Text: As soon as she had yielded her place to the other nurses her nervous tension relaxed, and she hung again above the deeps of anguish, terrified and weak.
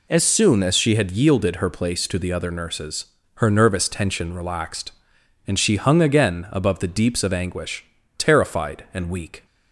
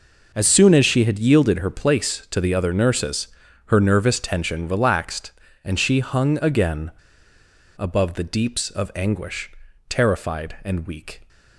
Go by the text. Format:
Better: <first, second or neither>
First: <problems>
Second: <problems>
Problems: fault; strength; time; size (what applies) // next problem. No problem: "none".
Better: first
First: pauses between "nurses" and "her"; slight; at 3.0 s; 0.34 s long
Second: pauses between "nurses" and "her"; at 3.2 s; 0.38 s long // pauses between "again" and "above"; noticeable; at 6.9 s; 0.87 s long